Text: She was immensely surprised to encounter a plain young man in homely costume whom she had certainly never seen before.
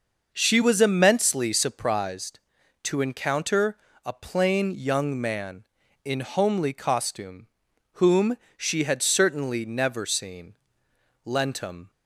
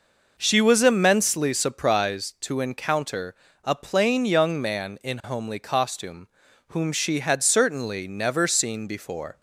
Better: second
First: pauses between "encounter" and "a"; slight; at 3.7 s; 0.30 s long // pauses between "costume" and "whom"; noticeable; at 7.4 s; 0.46 s long // pauses between "whom" and "she"; slight; at 8.3 s; 0.20 s long // says "lentum" for "before"; at 11.2 s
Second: pauses between "encounter" and "a"; slight; at 3.3 s; 0.30 s long // pauses between "costume" and "whom"; at 6.2 s; 0.40 s long

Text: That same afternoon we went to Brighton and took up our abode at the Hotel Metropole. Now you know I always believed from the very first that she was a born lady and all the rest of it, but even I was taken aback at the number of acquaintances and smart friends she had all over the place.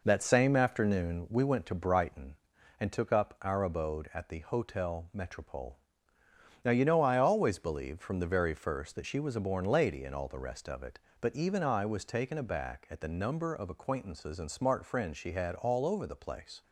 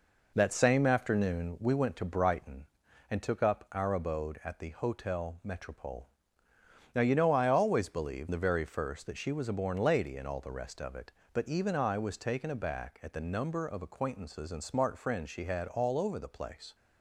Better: first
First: none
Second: skips "from"; at 8.3 s

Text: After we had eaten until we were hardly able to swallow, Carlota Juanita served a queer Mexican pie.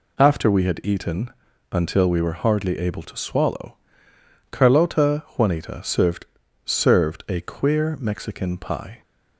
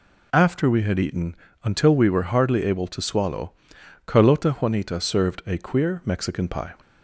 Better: second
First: pauses between "eaten" and "until"; at 1.3 s; 0.42 s long // says "served" twice; at 6.6 s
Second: pauses between "eaten" and "until"; slight; at 1.3 s; 0.30 s long

